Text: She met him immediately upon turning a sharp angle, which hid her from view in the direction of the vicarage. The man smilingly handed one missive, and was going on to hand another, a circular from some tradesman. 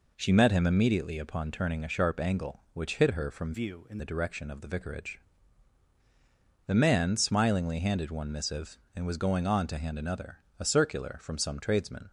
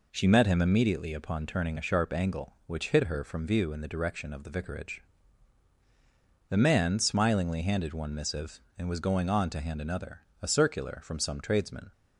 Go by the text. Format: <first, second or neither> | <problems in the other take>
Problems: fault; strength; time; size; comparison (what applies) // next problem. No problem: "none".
second | changes voice from "view" to "in"; from 3.5 to 3.9 s; 0.4 s long